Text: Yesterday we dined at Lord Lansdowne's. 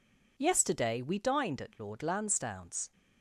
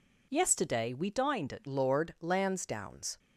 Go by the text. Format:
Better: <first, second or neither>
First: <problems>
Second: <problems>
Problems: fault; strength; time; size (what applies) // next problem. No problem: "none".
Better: first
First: none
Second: changes voice at "Lord"; from 1.6 s on; 1.5 s long